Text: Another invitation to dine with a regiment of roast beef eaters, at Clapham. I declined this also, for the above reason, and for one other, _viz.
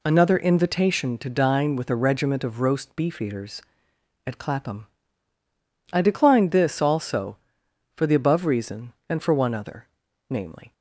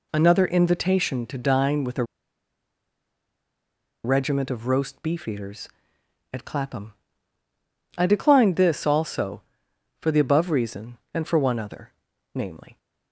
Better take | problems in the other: first | pauses between "a" and "regiment"; strong; at 2.0 s; 2.0 s long

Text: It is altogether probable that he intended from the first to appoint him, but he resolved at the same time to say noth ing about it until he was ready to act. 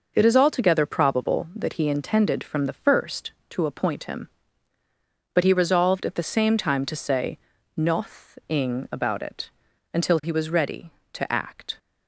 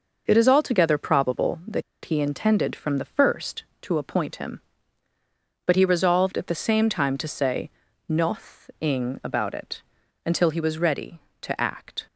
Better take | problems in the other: first | pauses between "that" and "he"; slight; at 1.8 s; 0.21 s long // pauses between "say" and "noth"; at 7.6 s; 0.38 s long; also in the first // pauses between "it" and "until"; at 9.8 s; 0.42 s long; also in the first

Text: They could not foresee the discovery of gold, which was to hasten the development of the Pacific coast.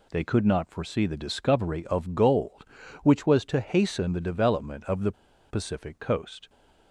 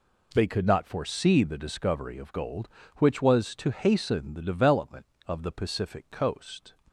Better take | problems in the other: second | pauses between "the" and "Pacific"; at 5.1 s; 0.37 s long

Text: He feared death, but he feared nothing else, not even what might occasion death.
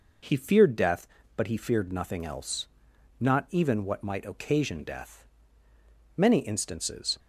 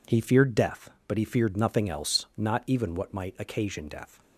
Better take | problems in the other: second | goes on to say "Many instances"; noticeable; from 6.1 s on; 1.0 s long

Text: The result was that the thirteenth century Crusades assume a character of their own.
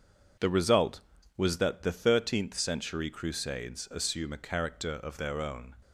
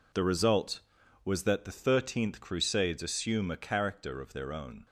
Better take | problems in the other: first | skips "century"; at 2.3 s

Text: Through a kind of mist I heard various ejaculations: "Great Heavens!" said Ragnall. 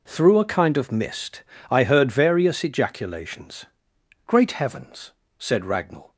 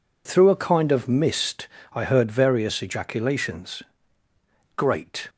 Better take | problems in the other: first | pauses between "mist" and "I"; slight; at 1.6 s; 0.24 s long; slight in the first // stops before "Heavens said Ragnall"; at 5.2 s

